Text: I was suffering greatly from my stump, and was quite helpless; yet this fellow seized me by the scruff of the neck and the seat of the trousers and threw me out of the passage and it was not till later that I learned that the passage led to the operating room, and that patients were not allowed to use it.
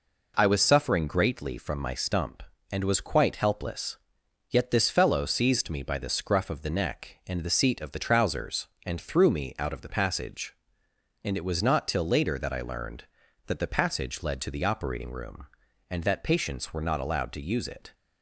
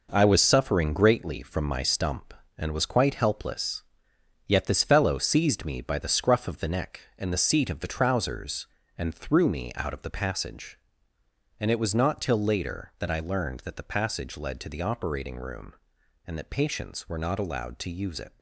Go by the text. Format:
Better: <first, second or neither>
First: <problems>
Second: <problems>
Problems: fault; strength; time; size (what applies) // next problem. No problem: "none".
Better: first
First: none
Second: gets quieter; strong; throughout; 8 dB